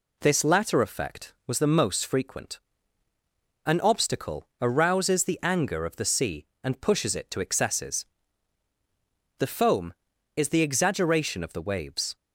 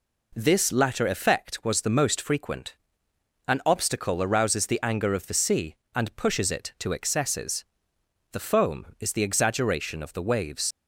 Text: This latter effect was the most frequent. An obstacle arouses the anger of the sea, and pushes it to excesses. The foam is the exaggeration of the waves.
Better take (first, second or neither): first